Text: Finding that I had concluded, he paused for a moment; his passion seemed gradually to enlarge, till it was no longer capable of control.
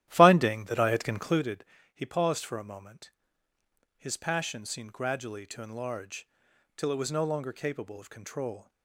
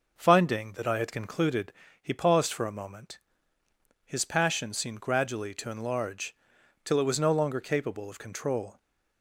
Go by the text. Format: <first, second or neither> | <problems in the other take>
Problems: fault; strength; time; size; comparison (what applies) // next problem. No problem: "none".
second | starts louder than the rest; strong; until 1.4 s; 13 dB